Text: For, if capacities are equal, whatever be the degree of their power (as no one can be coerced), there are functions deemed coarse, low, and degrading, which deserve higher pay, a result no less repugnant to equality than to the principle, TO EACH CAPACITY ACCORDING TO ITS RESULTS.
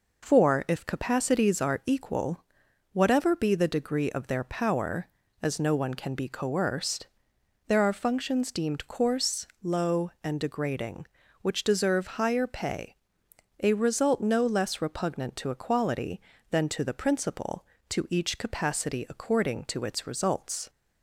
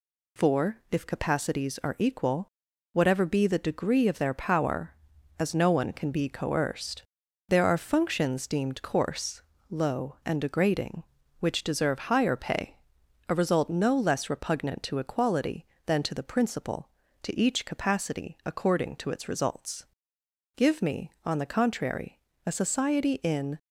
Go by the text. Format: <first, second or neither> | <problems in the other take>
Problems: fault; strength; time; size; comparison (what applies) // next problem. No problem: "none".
first | goes on to say "Give me on the contrary a society in"; strong; from 20.5 s on; 3.0 s long